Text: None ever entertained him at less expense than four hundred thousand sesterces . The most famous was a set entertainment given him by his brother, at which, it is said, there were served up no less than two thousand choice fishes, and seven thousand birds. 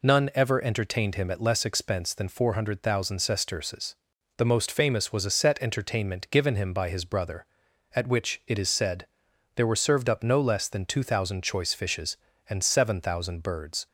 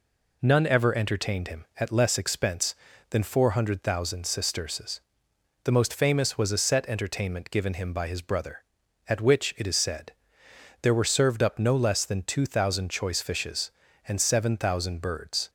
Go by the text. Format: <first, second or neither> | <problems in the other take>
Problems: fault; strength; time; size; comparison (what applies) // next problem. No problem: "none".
neither | none